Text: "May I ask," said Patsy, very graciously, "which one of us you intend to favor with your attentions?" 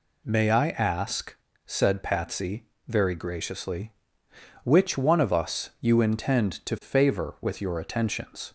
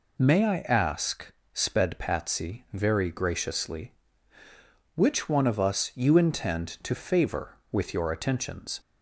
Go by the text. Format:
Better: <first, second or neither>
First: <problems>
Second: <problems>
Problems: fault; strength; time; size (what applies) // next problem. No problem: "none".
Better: first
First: none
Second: says "sped" for "said"; at 1.5 s